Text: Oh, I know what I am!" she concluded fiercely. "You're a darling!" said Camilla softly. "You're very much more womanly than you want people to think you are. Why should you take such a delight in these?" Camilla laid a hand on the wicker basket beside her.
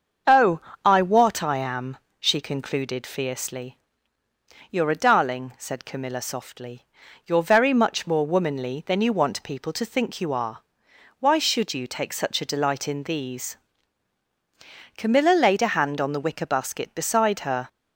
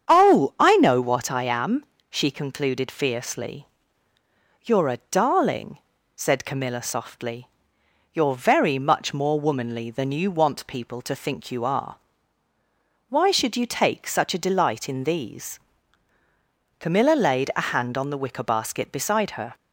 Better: second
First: starts louder than the rest; until 1.5 s; 7 dB // skips "know"; at 1.0 s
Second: starts louder than the rest; strong; until 1.1 s; 7.5 dB

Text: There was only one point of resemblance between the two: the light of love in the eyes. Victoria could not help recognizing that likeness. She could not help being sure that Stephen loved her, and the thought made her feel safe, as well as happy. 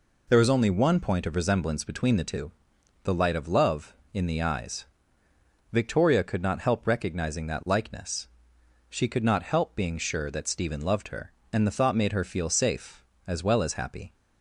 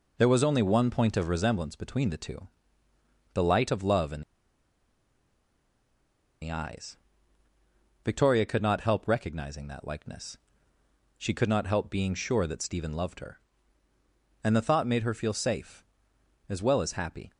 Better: first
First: none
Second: pauses between "in" and "the"; strong; at 4.2 s; 2.2 s long

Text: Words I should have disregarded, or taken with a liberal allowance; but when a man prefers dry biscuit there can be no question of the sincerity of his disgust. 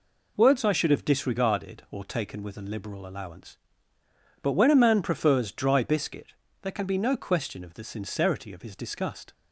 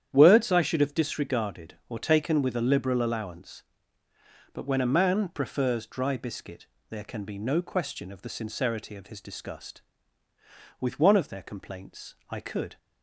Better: first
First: pauses between "biscuit" and "there"; slight; at 6.3 s; 0.30 s long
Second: starts louder than the rest; strong; until 1.1 s; 9.5 dB // pauses between "biscuit" and "there"; slight; at 6.6 s; 0.22 s long // goes on to say "With one of their complaints I could"; strong; from 10.7 s on; 1.9 s long

